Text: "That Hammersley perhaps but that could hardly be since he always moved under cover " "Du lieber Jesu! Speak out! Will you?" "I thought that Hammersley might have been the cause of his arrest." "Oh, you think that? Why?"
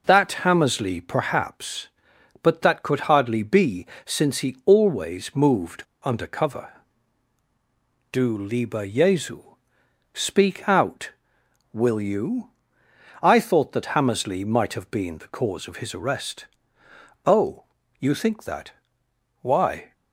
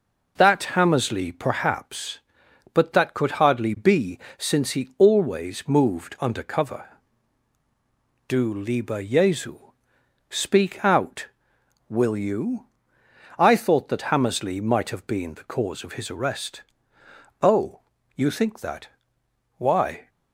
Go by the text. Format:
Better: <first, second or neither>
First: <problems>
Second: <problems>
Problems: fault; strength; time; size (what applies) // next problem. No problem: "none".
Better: second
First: starts louder than the rest; until 1.0 s; 6.5 dB // pauses between "be" and "since"; slight; at 3.8 s; 0.18 s long // pauses between "moved" and "under"; slight; at 5.8 s; 0.22 s long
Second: starts louder than the rest; until 1.3 s; 6.5 dB // pauses between "be" and "since"; slight; at 4.1 s; 0.18 s long